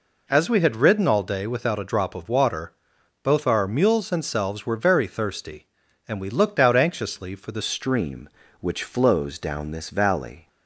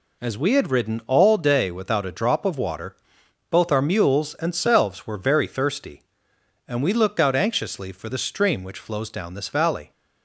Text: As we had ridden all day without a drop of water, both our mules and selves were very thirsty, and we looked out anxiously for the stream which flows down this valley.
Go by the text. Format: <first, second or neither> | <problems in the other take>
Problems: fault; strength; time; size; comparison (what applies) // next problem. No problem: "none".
second | changes voice at "stream"; from 7.6 s on; 2.8 s long